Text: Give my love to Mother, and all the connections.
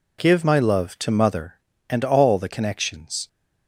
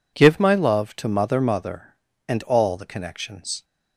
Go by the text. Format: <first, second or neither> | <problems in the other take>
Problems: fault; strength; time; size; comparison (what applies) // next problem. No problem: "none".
first | says "Mother" twice; at 1.4 s